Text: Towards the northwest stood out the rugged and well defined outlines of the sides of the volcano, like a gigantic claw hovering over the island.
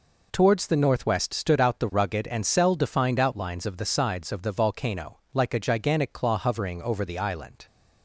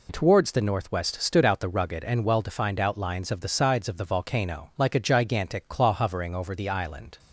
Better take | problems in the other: second | says "cell" for "well"; at 2.4 s

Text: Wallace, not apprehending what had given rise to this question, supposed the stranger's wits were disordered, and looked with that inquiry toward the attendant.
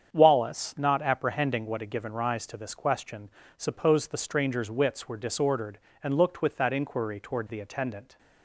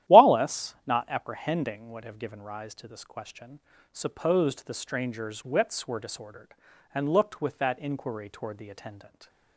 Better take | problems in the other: first | starts louder than the rest; strong; until 1.2 s; 12.5 dB; strong in the first // says "have" for "had"; at 2.0 s

